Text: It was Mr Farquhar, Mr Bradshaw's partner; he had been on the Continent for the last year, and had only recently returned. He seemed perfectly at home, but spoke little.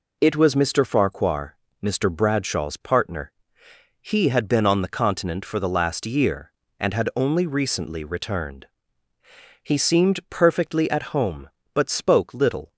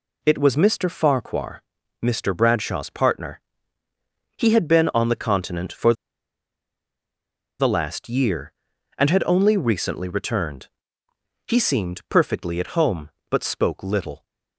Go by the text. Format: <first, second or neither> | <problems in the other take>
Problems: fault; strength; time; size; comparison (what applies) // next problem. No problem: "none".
first | pauses between "for" and "the"; strong; at 5.9 s; 1.6 s long